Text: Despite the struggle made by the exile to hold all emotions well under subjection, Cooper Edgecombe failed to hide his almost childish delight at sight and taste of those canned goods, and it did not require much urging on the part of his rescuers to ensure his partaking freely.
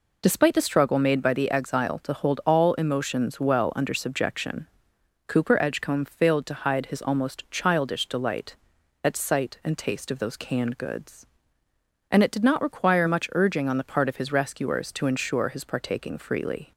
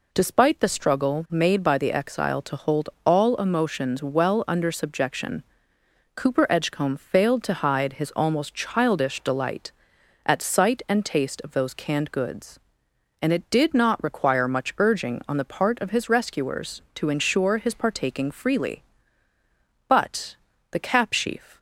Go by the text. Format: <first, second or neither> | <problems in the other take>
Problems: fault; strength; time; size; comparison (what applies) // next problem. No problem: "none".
first | pauses between "hold" and "all"; slight; at 2.8 s; 0.16 s long // goes on to say "But the cap sheaf"; strong; from 19.8 s on; 1.7 s long